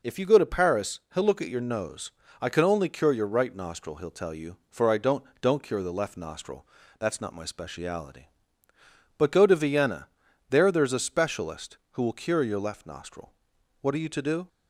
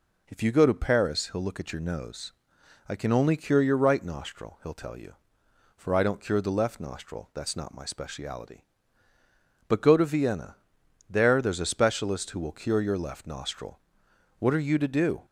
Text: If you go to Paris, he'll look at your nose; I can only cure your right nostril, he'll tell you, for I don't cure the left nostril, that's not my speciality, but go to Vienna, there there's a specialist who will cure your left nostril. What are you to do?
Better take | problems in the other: second | says "don't" twice; at 5.4 s

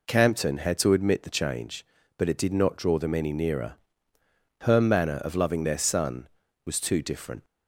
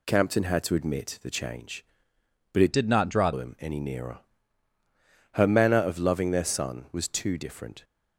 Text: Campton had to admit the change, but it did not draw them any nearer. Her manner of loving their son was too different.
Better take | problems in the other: first | changes voice from "did" to "draw"; from 2.7 to 3.3 s; 0.6 s long

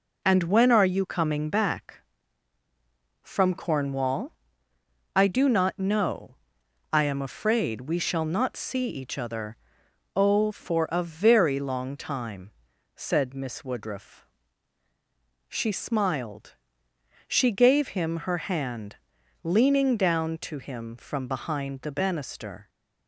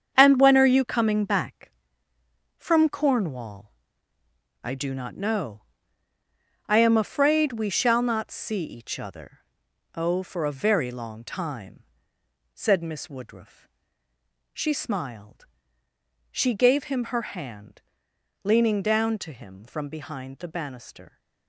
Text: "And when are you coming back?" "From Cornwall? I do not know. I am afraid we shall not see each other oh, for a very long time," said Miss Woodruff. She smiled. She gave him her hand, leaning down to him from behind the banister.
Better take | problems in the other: first | gets quieter; strong; throughout; 9 dB // pauses between "other" and "oh"; noticeable; at 9.3 s; 0.56 s long; noticeable in the first

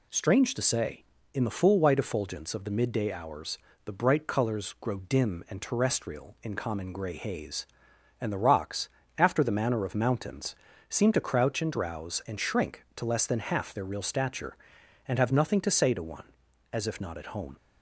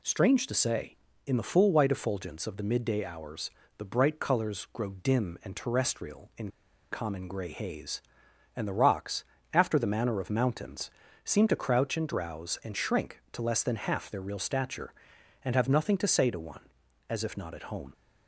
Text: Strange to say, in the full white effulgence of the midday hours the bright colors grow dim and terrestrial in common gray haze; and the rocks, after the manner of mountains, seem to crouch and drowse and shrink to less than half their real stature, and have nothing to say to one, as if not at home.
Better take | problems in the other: first | pauses between "hours" and "the"; slight; at 3.5 s; 0.26 s long; slight in the first // pauses between "in" and "common"; at 6.4 s; 0.42 s long

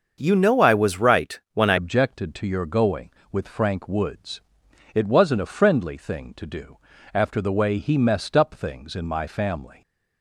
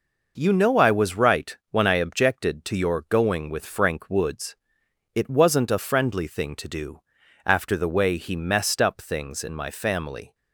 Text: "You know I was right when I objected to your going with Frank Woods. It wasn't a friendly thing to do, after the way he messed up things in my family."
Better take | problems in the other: second | starts louder than the rest; until 1.2 s; 6.5 dB // changes voice at "objected"; from 1.7 s on; 8.1 s long

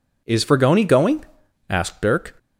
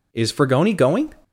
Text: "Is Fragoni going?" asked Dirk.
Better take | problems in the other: first | stops before "asked Dirk"; at 1.2 s

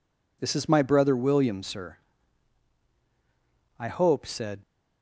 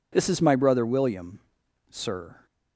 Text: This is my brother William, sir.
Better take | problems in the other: second | goes on to say "I hope said"; noticeable; from 3.7 s on; 0.84 s long

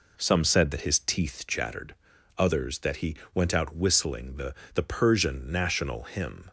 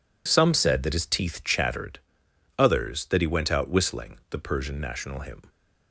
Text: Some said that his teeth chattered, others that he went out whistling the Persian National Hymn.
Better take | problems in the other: second | pauses between "he" and "went"; slight; at 3.1 s; 0.18 s long // says "the" twice; at 4.7 s

